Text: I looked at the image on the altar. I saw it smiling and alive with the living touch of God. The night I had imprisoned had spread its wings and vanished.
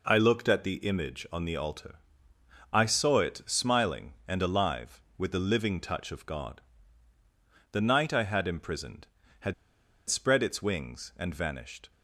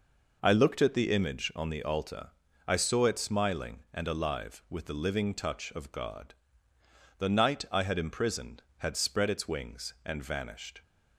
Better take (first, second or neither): second